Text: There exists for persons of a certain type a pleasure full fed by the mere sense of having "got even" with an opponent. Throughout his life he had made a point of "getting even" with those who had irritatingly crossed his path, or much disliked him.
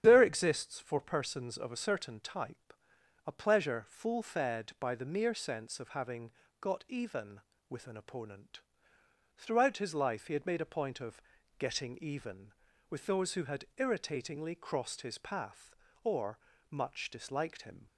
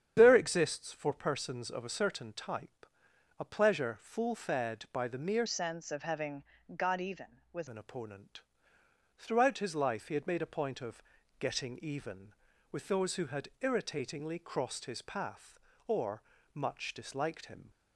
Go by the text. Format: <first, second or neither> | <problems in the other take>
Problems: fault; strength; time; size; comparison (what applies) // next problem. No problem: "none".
first | starts louder than the rest; strong; until 1.1 s; 8.5 dB; strong in the first // pauses between "type" and "a"; noticeable; at 2.8 s; 0.52 s long; noticeable in the first // changes voice from "sense" to "with"; from 5.4 to 7.6 s; 2.2 s long // pauses between "having" and "got"; slight; at 6.4 s; 0.32 s long; slight in the first // pauses between "of" and "getting"; slight; at 11.0 s; 0.34 s long; slight in the first // pauses between "or" and "much"; slight; at 16.2 s; 0.32 s long; slight in the first